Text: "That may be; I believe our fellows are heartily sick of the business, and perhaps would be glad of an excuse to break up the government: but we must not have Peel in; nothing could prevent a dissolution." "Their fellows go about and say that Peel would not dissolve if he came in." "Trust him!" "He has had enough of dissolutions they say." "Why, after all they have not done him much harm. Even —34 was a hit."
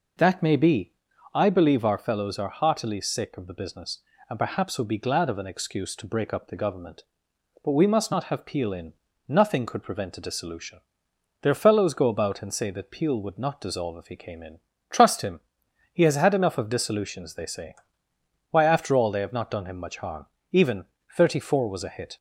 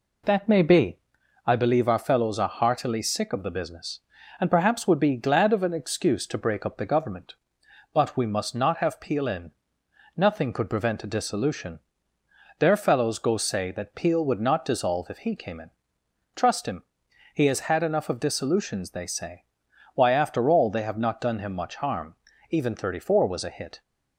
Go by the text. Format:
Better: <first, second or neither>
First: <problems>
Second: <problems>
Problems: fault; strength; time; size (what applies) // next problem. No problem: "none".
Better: first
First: none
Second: skips "about and"; at 13.3 s